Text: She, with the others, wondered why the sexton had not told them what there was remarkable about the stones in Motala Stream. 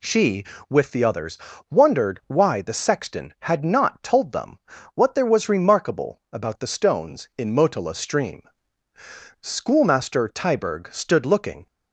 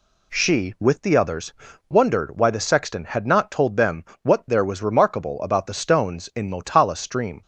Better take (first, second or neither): second